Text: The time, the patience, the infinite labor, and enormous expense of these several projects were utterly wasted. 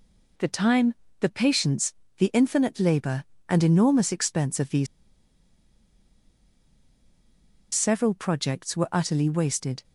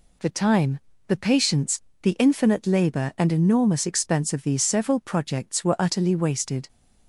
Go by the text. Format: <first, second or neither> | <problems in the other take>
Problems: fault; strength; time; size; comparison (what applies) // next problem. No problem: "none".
second | pauses between "these" and "several"; strong; at 4.8 s; 2.8 s long